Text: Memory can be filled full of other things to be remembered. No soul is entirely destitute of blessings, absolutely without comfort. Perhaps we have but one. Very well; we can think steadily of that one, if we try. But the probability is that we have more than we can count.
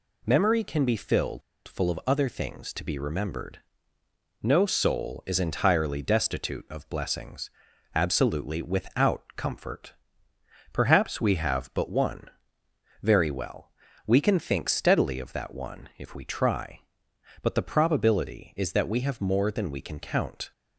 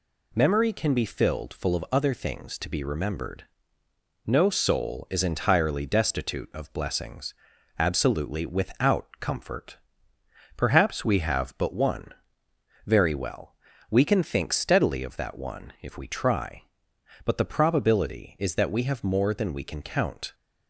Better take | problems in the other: second | pauses between "filled" and "full"; slight; at 1.4 s; 0.26 s long

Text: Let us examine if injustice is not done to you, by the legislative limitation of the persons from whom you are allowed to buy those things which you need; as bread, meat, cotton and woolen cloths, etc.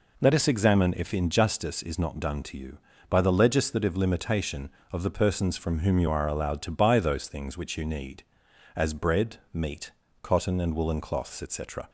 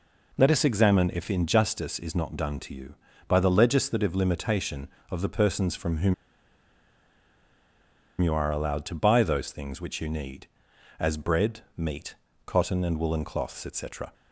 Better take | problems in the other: first | pauses between "whom" and "you"; strong; at 6.1 s; 2.0 s long

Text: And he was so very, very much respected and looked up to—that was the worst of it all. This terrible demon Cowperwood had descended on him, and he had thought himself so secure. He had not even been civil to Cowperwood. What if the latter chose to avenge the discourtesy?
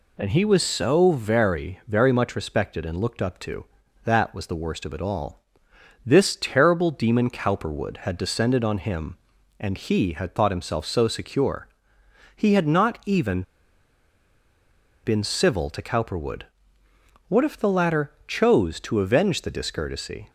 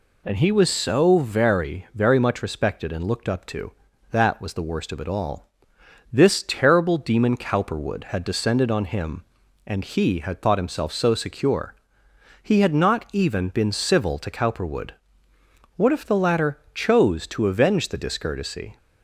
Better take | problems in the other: second | pauses between "even" and "been"; strong; at 13.4 s; 1.6 s long

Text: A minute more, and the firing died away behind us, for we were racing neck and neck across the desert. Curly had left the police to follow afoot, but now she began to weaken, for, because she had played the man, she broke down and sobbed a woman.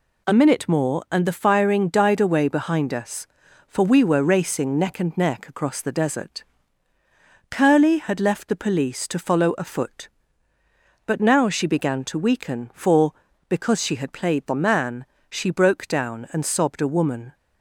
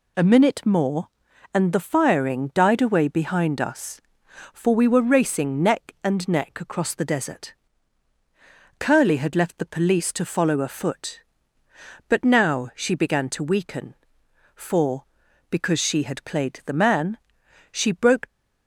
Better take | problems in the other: first | stops before "down and sobbed a woman"; at 18.2 s

